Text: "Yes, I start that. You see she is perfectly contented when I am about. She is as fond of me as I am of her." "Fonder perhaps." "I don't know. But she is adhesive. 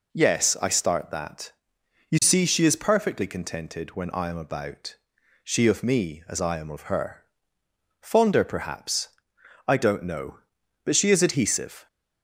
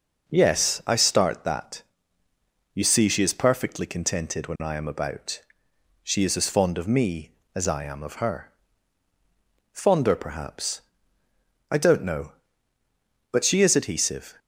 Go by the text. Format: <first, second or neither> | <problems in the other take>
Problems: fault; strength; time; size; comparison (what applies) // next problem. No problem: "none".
second | skips "is as fond"; at 5.6 s